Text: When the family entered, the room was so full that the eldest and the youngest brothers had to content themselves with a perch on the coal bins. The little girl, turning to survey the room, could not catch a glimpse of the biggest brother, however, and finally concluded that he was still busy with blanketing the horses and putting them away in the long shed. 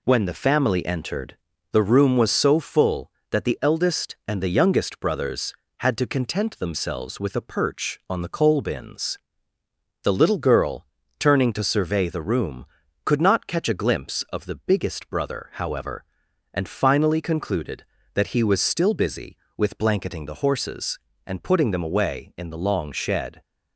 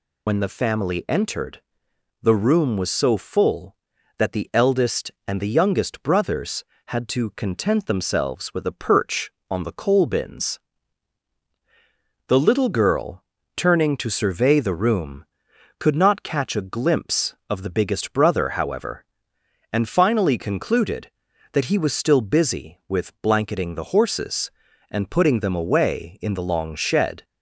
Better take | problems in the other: first | loses the start of "When"; at 0.2 s; 70 ms

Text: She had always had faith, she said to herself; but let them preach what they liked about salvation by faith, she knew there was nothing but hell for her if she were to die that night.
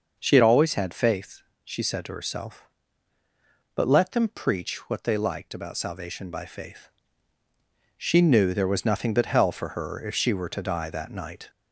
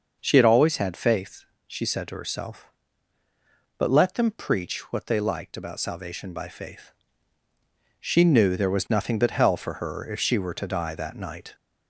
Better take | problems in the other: neither | starts louder than the rest; the same in both

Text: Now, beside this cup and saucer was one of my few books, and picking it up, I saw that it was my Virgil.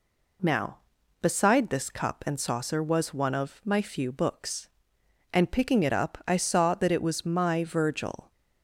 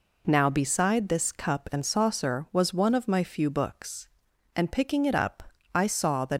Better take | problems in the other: first | stops before "it was my Virgil"; at 6.3 s

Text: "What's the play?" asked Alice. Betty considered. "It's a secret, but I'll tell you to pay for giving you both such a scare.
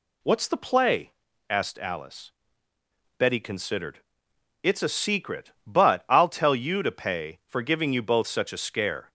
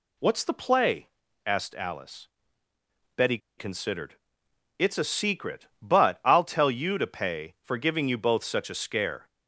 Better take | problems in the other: first | pauses between "Betty" and "considered"; slight; at 3.3 s; 0.20 s long

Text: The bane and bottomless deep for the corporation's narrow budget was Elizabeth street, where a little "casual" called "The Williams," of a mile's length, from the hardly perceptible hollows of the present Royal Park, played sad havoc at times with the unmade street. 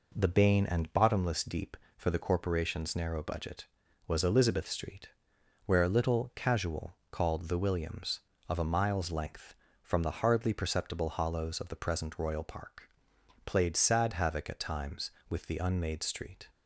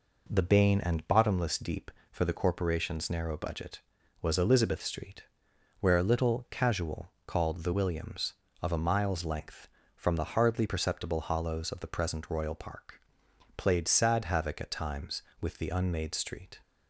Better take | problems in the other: neither | none

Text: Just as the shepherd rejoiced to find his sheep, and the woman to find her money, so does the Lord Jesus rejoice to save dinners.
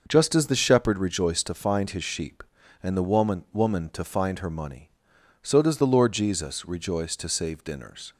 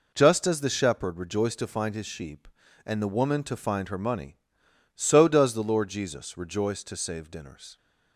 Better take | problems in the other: second | says "woman" twice; at 3.5 s

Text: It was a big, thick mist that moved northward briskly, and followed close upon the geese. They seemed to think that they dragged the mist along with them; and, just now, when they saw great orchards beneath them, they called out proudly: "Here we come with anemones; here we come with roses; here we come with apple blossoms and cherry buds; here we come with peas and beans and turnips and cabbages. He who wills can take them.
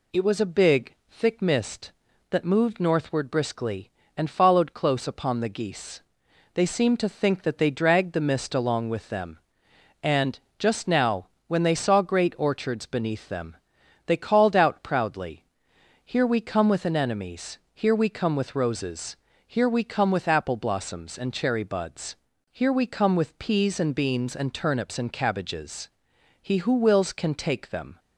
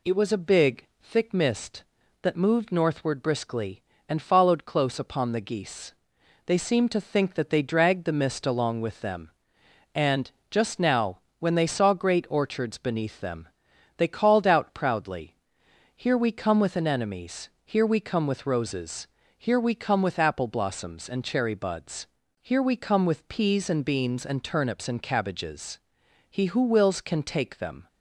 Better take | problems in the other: neither | none

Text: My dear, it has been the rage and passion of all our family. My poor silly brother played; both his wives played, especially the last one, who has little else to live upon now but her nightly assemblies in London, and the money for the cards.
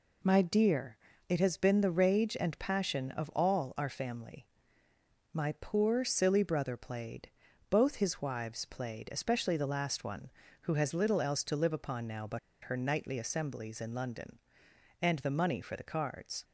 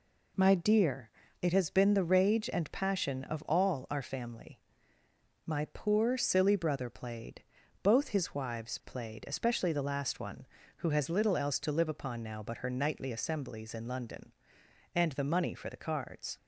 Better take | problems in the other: second | pauses between "but" and "her"; slight; at 12.3 s; 0.24 s long

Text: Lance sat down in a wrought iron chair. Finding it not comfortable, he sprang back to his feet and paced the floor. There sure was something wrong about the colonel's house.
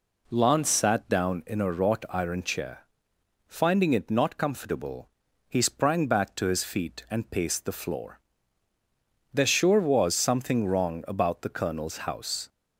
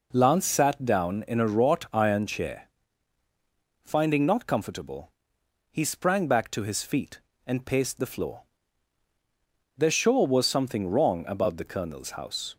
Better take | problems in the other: first | skips "it"; at 4.2 s

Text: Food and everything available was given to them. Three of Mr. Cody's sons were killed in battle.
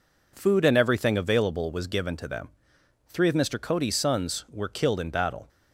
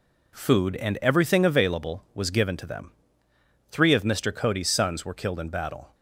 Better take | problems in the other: neither | none

